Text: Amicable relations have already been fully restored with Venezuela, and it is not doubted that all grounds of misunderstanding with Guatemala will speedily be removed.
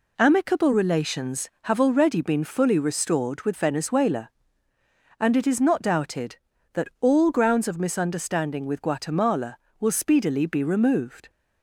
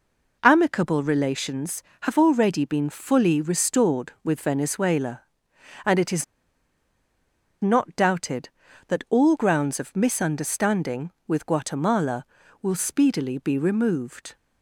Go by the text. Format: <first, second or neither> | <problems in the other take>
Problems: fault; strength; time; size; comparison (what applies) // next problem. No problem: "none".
first | pauses between "is" and "not"; strong; at 6.2 s; 1.3 s long